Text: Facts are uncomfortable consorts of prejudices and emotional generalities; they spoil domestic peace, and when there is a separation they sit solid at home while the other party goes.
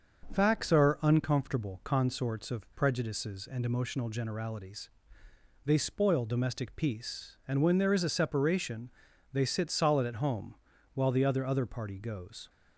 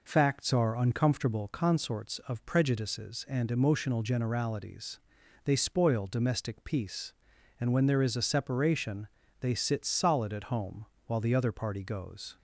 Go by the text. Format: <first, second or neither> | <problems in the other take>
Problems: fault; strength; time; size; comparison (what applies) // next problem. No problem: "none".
second | starts louder than the rest; until 1.3 s; 6.5 dB // pauses between "separation" and "they"; at 8.9 s; 0.40 s long; slight in the second // pauses between "home" and "while"; at 10.5 s; 0.40 s long; slight in the second // says "other" twice; at 11.4 s